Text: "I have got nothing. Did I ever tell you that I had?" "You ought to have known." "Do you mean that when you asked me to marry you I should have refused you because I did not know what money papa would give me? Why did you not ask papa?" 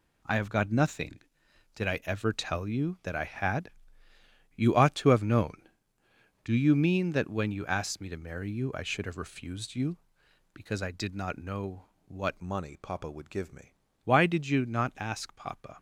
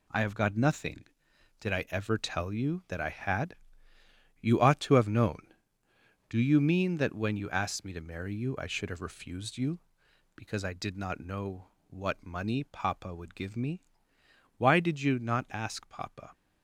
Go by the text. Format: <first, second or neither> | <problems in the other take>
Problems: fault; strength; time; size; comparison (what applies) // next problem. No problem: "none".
second | pauses between "know" and "what"; slight; at 11.8 s; 0.24 s long; slight in the second // changes voice from "money" to "me"; from 12.4 to 13.7 s; 1.3 s long